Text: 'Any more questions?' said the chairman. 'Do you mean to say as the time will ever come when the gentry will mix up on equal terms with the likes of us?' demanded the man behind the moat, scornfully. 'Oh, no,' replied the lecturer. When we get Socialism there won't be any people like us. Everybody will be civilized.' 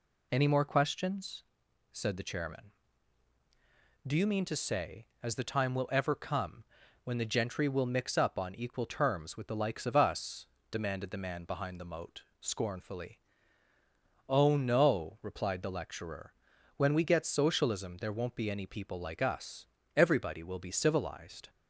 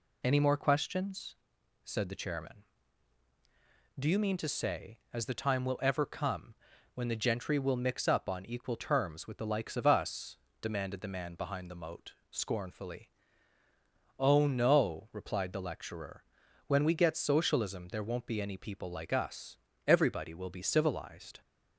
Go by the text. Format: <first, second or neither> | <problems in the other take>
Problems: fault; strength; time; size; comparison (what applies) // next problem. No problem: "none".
neither | pauses between "come" and "when"; the same in both